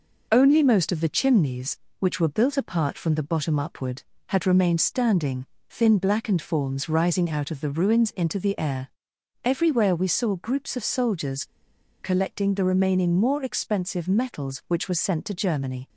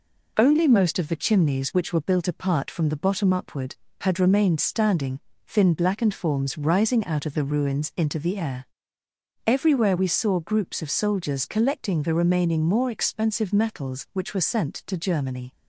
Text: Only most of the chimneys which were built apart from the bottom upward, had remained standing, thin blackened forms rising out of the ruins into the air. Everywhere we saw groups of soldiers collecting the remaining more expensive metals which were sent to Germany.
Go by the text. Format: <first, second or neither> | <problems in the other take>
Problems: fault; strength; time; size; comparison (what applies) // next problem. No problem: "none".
second | pauses between "soldiers" and "collecting"; noticeable; at 11.4 s; 0.57 s long